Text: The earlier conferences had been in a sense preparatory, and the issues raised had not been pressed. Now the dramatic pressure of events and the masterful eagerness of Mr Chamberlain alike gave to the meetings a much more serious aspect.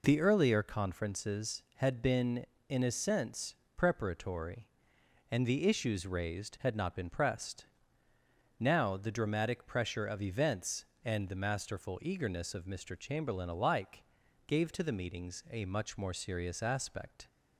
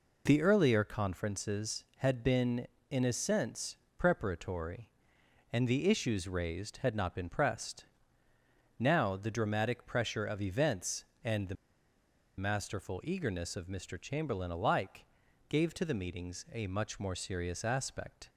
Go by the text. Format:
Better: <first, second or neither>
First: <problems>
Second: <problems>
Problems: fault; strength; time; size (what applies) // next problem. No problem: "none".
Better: first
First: pauses between "sense" and "preparatory"; slight; at 3.5 s; 0.20 s long // pauses between "alike" and "gave"; at 14.0 s; 0.44 s long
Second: pauses between "sense" and "preparatory"; slight; at 3.7 s; 0.20 s long // pauses between "the" and "masterful"; noticeable; at 11.5 s; 0.83 s long // pauses between "alike" and "gave"; at 15.0 s; 0.44 s long